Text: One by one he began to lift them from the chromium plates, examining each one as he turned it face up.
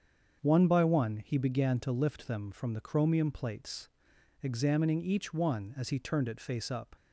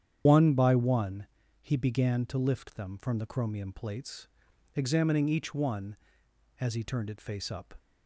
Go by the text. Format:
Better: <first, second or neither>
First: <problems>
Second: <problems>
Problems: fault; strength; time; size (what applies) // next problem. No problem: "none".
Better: first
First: starts louder than the rest; until 1.4 s; 7 dB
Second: loses the start of "One"; at 0.2 s; 105 ms // starts louder than the rest; strong; until 1.2 s; 9 dB // pauses between "one" and "he"; slight; at 1.2 s; 0.34 s long